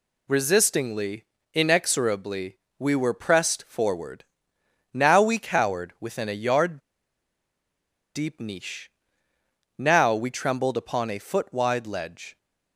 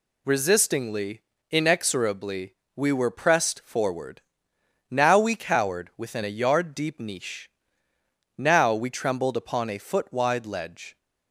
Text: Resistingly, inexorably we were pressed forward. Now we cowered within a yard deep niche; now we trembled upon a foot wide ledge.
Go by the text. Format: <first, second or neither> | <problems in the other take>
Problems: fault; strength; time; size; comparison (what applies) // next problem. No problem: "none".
second | pauses between "inexorably" and "we"; slight; at 2.5 s; 0.20 s long; slight in the second // pauses between "yard" and "deep"; strong; at 6.7 s; 1.3 s long